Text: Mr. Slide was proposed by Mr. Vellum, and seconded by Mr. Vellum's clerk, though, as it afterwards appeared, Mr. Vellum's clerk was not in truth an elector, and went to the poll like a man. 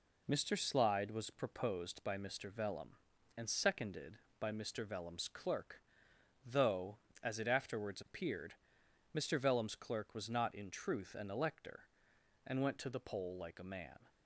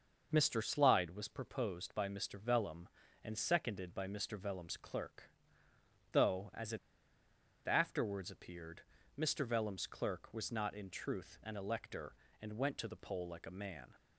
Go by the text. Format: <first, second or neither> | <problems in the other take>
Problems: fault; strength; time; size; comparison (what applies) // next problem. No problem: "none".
first | starts louder than the rest; noticeable; until 1.3 s; 6 dB // pauses between "it" and "afterwards"; noticeable; at 6.7 s; 0.88 s long